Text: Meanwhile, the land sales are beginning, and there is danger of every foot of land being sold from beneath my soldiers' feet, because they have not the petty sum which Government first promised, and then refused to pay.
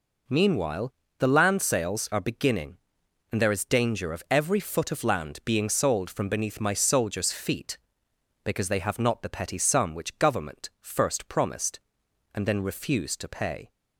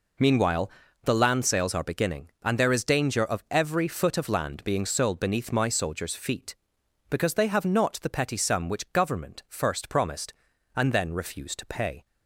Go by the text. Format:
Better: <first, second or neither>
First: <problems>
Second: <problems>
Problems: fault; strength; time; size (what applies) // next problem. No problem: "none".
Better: first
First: none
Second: skips "from"; at 5.1 s